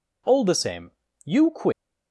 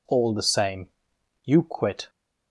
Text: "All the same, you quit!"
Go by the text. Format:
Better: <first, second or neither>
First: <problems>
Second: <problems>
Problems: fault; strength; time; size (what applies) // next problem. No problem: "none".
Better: second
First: leaves "quit" unfinished; at 1.7 s; 100 ms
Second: none